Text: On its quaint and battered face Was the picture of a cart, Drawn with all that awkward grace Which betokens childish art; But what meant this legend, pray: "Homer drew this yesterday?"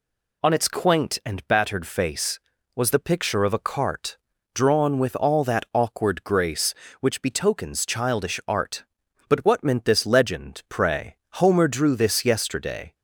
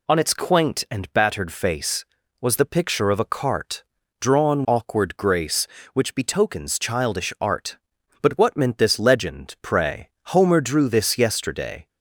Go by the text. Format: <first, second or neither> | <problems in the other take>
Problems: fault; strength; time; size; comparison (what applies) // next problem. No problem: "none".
first | skips "with all that"; at 4.6 s